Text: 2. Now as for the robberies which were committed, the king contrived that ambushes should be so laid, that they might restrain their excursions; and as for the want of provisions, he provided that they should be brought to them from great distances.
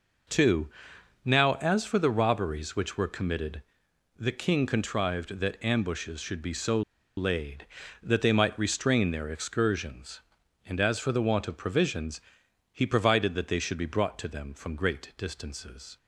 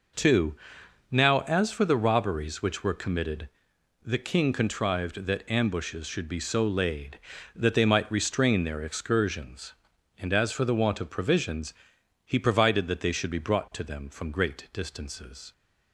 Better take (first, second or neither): second